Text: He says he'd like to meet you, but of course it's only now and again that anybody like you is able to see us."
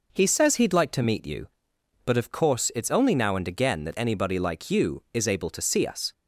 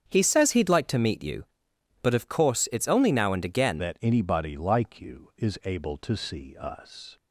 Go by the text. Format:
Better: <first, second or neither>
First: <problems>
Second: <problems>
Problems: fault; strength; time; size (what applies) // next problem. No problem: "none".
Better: first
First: none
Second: starts louder than the rest; strong; until 1.1 s; 8.5 dB // changes voice at "that"; from 3.7 s on; 3.4 s long